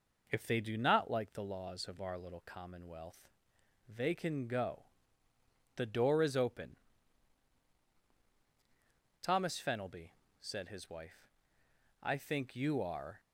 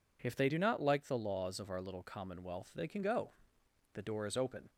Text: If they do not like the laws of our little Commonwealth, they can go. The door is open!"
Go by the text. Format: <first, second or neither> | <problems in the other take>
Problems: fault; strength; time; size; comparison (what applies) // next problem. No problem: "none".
second | goes on to say "Thomas Fenelby said his wife I think you are"; strong; from 9.2 s on; 3.9 s long